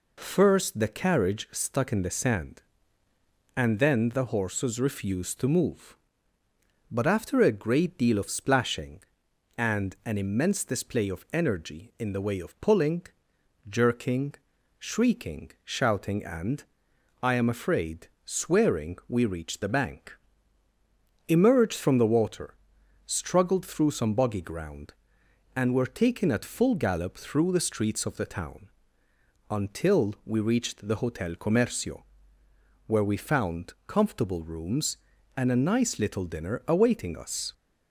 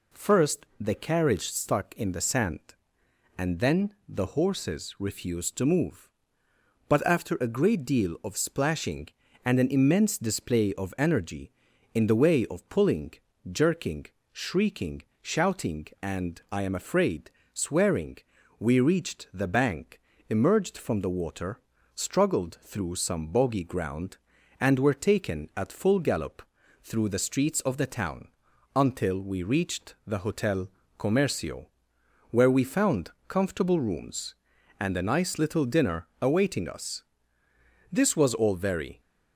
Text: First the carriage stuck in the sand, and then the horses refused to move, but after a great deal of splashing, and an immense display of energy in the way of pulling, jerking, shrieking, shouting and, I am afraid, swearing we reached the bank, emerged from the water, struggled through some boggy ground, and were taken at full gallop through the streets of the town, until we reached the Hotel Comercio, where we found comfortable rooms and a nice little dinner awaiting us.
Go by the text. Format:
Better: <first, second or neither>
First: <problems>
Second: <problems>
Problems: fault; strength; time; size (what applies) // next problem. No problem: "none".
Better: first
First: none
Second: pauses between "swearing" and "we"; at 18.1 s; 0.42 s long // pauses between "gallop" and "through"; at 26.4 s; 0.42 s long // pauses between "Hotel" and "Comercio"; slight; at 30.6 s; 0.30 s long // pauses between "found" and "comfortable"; slight; at 33.0 s; 0.18 s long // goes on to say "This was all very"; noticeable; from 37.9 s on; 1.0 s long